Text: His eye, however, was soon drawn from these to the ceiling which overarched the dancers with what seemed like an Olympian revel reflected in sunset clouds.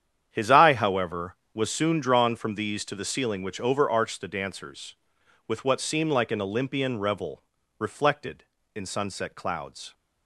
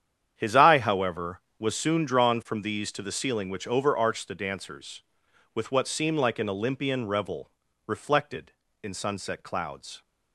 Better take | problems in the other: neither | starts louder than the rest; strong; the same in both // pauses between "revel" and "reflected"; slight; the same in both

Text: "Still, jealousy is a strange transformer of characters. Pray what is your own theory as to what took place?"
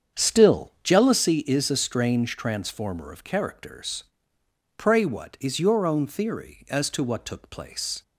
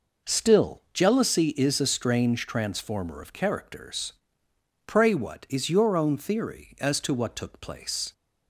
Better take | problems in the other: second | starts louder than the rest; strong; until 1.4 s; 7.5 dB

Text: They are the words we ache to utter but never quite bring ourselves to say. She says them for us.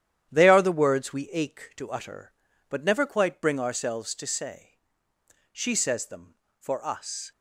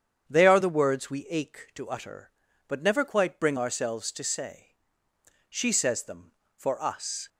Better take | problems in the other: second | gets quieter; strong; throughout; 7.5 dB // starts louder than the rest; strong; until 1.3 s; 10.5 dB; strong in the second

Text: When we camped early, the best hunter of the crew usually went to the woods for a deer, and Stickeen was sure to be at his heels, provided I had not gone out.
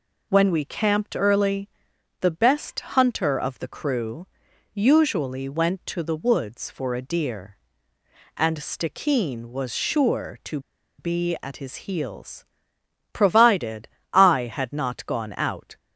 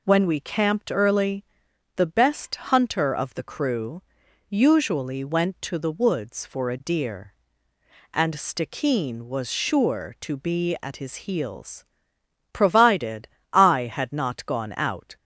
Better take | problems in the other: second | pauses between "crew" and "usually"; noticeable; at 4.2 s; 0.46 s long; noticeable in the second // pauses between "to" and "be"; at 10.5 s; 0.39 s long // pauses between "provided" and "I"; slight; at 13.8 s; 0.24 s long; slight in the second

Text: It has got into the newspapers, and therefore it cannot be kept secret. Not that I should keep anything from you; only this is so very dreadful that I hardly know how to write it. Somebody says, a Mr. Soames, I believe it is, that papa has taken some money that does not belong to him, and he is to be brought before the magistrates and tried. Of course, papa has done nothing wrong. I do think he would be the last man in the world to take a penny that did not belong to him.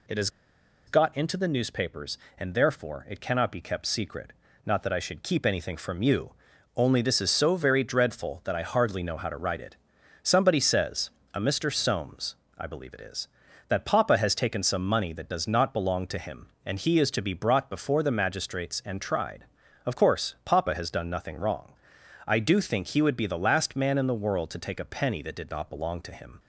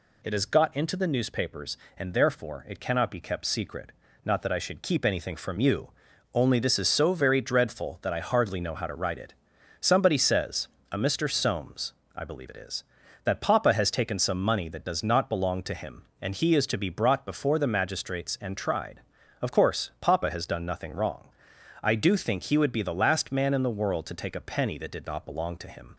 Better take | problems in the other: second | pauses between "has" and "got"; noticeable; at 0.2 s; 0.57 s long

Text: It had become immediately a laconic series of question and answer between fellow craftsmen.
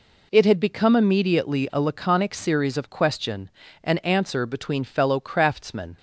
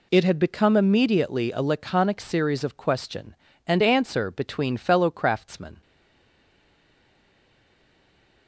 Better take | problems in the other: first | stays silent after the last word; strong; from 5.8 s on; 2.6 s long

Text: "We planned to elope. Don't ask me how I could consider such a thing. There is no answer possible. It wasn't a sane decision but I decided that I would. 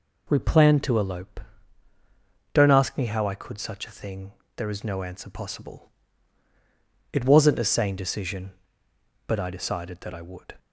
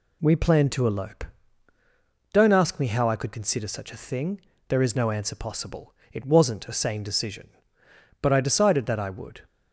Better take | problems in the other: second | skips "consider"; at 3.5 s

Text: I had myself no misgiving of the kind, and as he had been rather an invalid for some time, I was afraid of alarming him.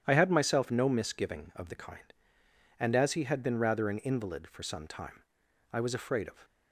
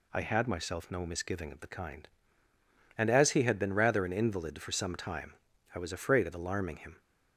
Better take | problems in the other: second | starts louder than the rest; strong; until 1.0 s; 9.5 dB // stops before "alarming him"; at 6.4 s

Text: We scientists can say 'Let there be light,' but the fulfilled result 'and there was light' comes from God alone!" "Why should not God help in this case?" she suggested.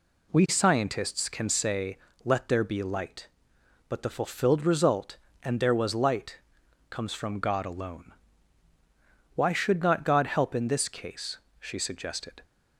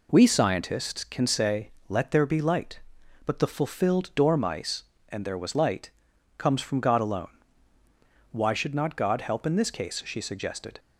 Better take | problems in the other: first | pauses between "say" and "Let"; slight; at 1.7 s; 0.18 s long; slight in the first // says "dormice" for "result"; at 4.1 s // pauses between "light" and "comes"; noticeable; at 5.9 s; 0.48 s long; noticeable in the first

